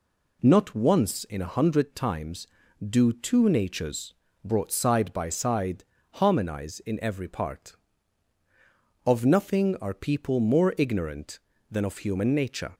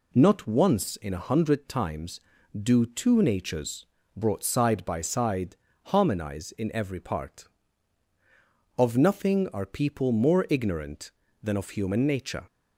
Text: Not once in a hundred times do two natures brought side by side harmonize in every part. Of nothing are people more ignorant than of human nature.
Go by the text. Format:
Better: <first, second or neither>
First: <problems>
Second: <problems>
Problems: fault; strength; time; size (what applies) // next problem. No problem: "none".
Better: neither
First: pauses between "natures" and "brought"; slight; at 4.1 s; 0.30 s long // pauses between "side" and "harmonize"; slight; at 5.8 s; 0.28 s long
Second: pauses between "natures" and "brought"; slight; at 3.8 s; 0.30 s long // pauses between "side" and "harmonize"; slight; at 5.5 s; 0.28 s long